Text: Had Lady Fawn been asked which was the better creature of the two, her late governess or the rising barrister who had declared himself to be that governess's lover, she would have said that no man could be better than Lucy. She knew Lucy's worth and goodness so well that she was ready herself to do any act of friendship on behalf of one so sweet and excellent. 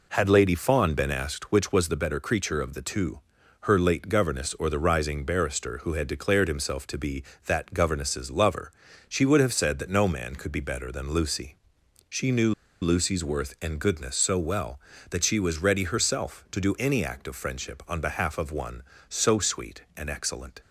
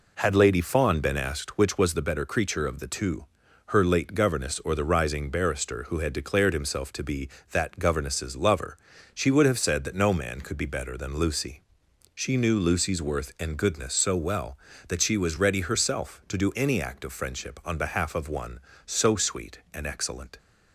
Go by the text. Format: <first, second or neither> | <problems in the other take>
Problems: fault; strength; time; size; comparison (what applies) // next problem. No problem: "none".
second | pauses between "knew" and "Lucy's"; slight; at 12.5 s; 0.28 s long